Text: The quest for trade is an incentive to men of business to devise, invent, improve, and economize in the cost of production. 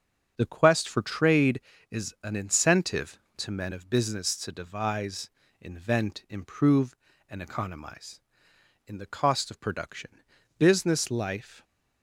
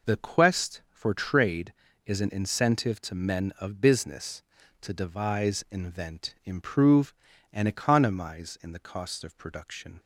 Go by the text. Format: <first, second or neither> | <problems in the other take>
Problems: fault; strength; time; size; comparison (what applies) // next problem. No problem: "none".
second | starts louder than the rest; until 1.3 s; 7 dB // goes on to say "Business life"; noticeable; from 10.5 s on; 1.0 s long